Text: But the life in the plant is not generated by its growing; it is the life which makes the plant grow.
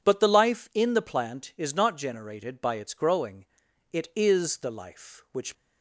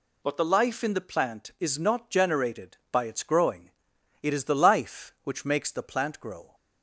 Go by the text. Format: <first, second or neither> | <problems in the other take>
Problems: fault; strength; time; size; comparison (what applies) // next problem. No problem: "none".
second | stops before "makes the plant grow"; at 5.5 s